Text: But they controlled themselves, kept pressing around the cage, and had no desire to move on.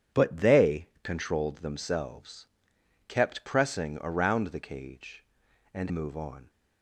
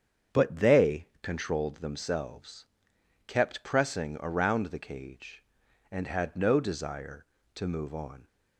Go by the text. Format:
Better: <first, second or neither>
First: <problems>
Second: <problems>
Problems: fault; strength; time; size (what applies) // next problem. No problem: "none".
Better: second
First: starts louder than the rest; strong; until 1.2 s; 8.5 dB // skips "had no desire to"; at 5.8 s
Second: starts louder than the rest; strong; until 1.4 s; 7.5 dB